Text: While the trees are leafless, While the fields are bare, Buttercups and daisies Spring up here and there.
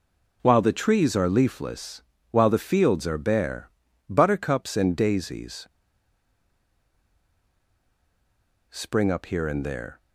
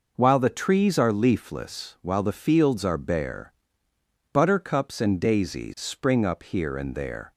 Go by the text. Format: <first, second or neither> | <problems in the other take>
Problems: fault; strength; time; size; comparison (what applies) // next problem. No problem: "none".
second | pauses between "daisies" and "Spring"; strong; at 5.6 s; 3.0 s long